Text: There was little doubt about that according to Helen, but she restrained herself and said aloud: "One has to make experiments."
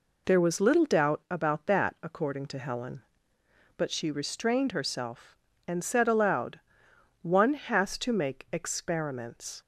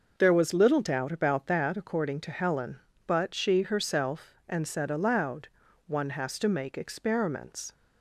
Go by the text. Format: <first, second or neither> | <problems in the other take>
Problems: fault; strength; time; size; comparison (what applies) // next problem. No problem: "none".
first | skips "restrained"; at 3.6 s